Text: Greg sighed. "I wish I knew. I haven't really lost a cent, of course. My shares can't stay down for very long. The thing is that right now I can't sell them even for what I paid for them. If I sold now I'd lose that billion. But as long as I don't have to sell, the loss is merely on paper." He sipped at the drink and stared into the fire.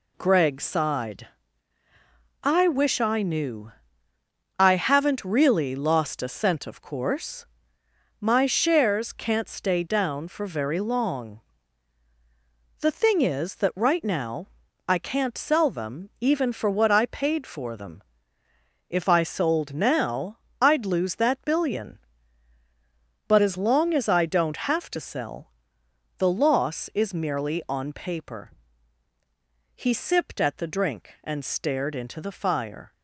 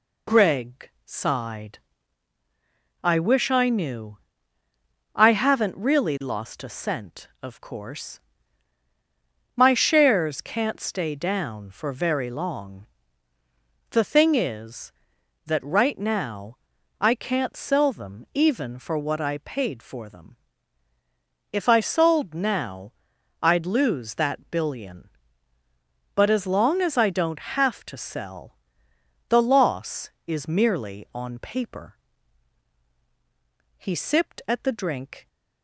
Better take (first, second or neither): first